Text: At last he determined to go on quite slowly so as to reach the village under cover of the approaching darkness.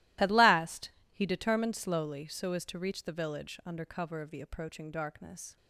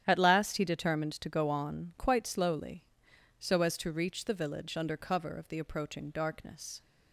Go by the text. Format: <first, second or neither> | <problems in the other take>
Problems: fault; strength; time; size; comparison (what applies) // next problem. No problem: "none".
second | starts louder than the rest; strong; until 1.4 s; 16 dB; strong in the second // pauses between "last" and "he"; slight; at 0.8 s; 0.22 s long // skips "to go on quite"; at 1.7 s